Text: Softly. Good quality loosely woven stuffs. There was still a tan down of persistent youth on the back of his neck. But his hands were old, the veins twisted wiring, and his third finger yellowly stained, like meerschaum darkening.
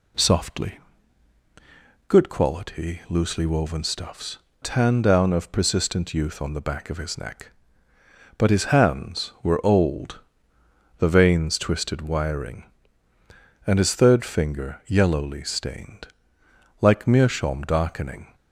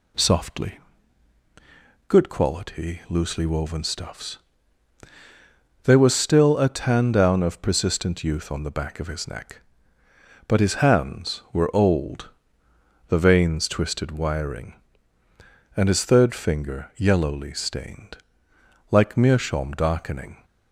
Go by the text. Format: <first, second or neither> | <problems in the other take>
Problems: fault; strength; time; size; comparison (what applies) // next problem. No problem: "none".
second | skips "There was still a"; at 4.4 s